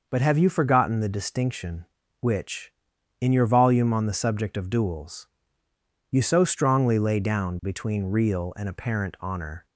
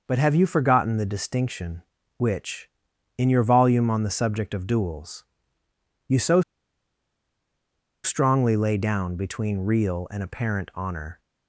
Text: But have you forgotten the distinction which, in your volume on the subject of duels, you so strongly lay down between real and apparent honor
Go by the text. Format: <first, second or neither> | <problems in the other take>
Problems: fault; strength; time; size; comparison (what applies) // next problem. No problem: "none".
first | pauses between "so" and "strongly"; strong; at 6.4 s; 1.6 s long